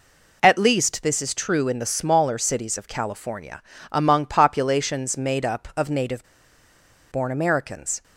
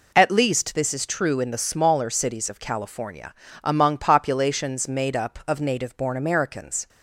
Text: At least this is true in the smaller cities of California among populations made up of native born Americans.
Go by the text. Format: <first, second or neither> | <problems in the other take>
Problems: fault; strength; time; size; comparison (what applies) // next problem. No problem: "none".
second | pauses between "California" and "among"; slight; at 3.6 s; 0.30 s long; slight in the second // pauses between "native" and "born"; noticeable; at 6.2 s; 0.85 s long